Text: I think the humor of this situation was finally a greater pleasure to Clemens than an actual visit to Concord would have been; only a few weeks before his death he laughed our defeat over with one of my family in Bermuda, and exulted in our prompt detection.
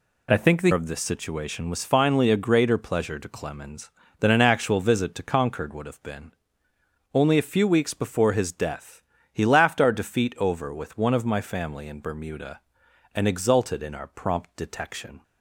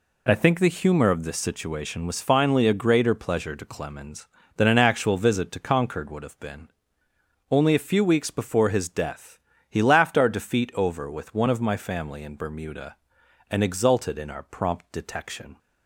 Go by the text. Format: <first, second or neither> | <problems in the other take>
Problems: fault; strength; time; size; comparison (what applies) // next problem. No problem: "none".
second | skips "humor"; at 0.7 s // pauses between "death" and "he"; slight; at 9.0 s; 0.30 s long; slight in the second